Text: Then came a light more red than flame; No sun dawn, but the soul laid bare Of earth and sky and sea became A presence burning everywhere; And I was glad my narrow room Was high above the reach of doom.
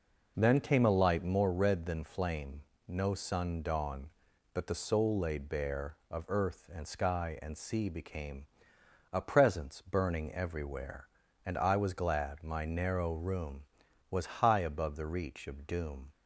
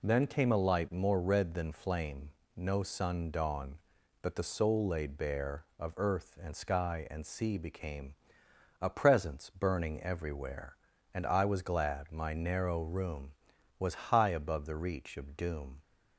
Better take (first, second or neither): second